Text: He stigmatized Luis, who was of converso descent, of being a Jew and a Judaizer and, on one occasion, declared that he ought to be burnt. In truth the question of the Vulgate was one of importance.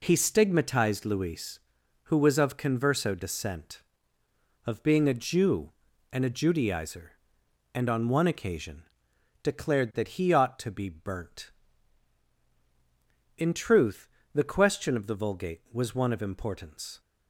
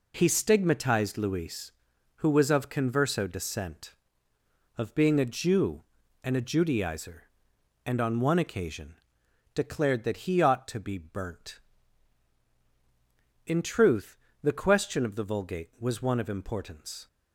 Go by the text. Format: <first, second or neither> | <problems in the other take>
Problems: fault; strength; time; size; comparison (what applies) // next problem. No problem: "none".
neither | pauses between "truth" and "the"; slight; the same in both